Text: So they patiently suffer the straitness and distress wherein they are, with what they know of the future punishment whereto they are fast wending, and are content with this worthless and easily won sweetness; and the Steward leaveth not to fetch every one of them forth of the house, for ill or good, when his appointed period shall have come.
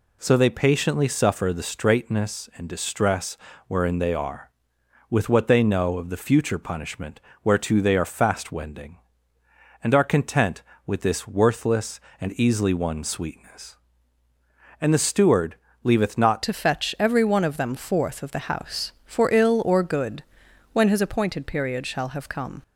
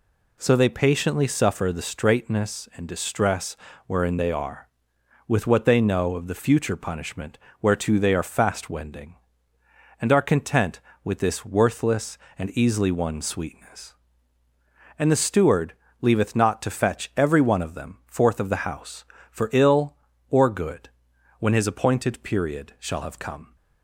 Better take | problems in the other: second | pauses between "distress" and "wherein"; slight; at 3.3 s; 0.30 s long; slight in the second // pauses between "punishment" and "whereto"; slight; at 7.2 s; 0.20 s long; slight in the second // pauses between "Steward" and "leaveth"; slight; at 15.5 s; 0.28 s long; slight in the second // changes voice at "to"; from 16.4 s on; 6.2 s long

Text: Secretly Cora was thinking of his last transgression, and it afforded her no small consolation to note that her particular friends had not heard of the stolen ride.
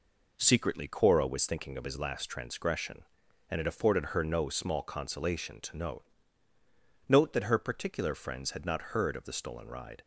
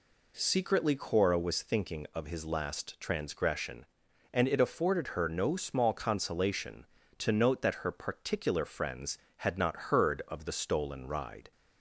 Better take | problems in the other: second | says "note" twice; at 7.0 s

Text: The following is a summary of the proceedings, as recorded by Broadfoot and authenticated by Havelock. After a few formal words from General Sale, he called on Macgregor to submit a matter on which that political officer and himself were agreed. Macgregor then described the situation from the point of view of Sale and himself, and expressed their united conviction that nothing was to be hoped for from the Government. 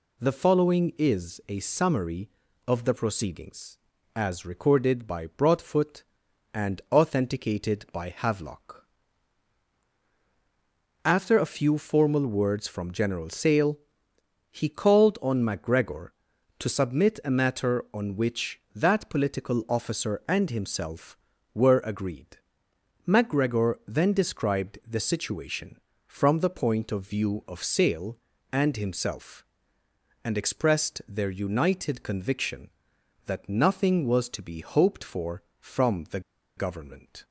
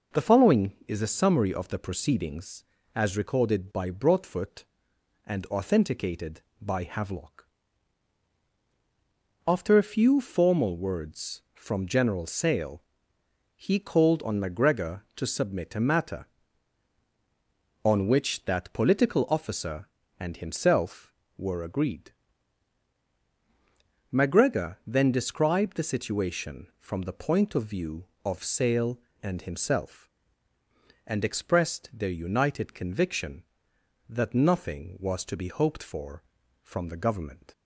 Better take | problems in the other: second | pauses between "the" and "Government"; at 36.1 s; 0.37 s long

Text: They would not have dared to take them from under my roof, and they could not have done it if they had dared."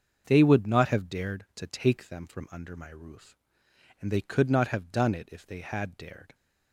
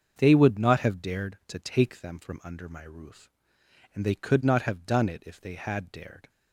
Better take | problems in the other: neither | starts louder than the rest; the same in both

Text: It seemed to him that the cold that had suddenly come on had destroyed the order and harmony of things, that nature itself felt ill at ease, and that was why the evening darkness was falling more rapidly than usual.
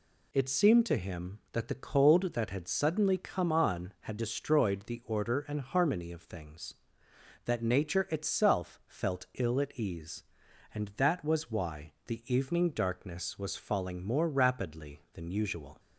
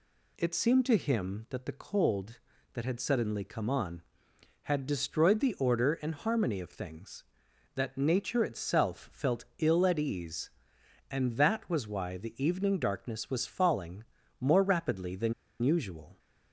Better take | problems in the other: first | pauses between "falling" and "more"; slight; at 14.0 s; 0.36 s long // pauses between "than" and "usual"; slight; at 15.3 s; 0.29 s long

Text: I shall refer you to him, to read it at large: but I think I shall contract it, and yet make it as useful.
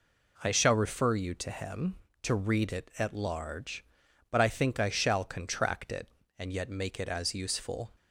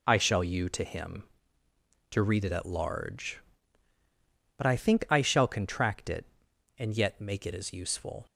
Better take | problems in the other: first | skips "refer"; at 0.4 s

